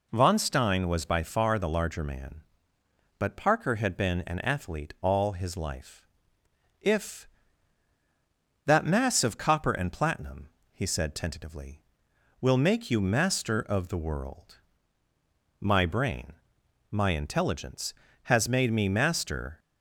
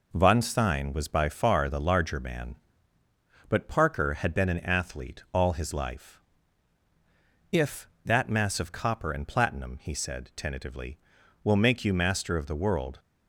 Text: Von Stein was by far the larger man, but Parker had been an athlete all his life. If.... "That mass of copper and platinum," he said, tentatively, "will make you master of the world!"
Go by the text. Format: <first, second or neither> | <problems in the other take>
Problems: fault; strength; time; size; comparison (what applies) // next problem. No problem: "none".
second | goes on to say "My brain my intelligence has made me master"; strong; from 15.6 s on; 3.9 s long